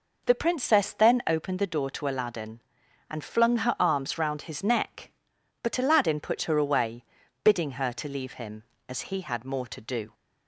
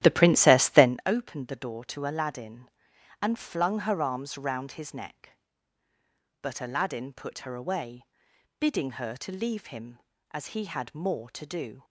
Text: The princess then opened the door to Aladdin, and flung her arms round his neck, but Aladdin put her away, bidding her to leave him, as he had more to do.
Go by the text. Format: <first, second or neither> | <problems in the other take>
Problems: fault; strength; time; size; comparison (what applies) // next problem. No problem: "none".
first | starts louder than the rest; strong; until 0.9 s; 12.5 dB